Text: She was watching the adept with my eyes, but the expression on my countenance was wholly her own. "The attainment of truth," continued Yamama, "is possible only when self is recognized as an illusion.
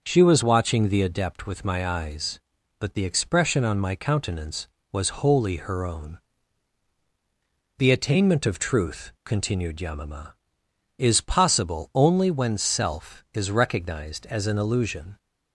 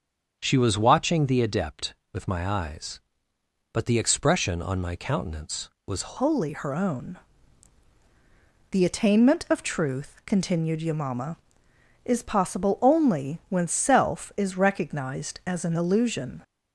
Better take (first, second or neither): first